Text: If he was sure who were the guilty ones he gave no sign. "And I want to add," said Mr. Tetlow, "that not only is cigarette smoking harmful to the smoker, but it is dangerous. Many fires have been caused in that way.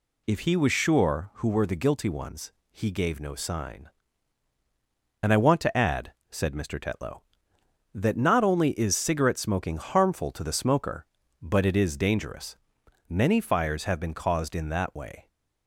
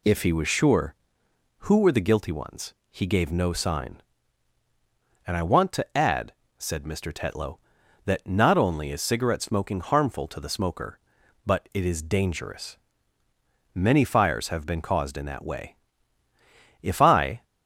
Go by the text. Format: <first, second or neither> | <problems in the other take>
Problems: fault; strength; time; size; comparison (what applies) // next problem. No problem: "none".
first | pauses between "ones" and "he"; slight; at 2.7 s; 0.18 s long; slight in the first // goes on to say "If I"; noticeable; from 16.8 s on; 0.62 s long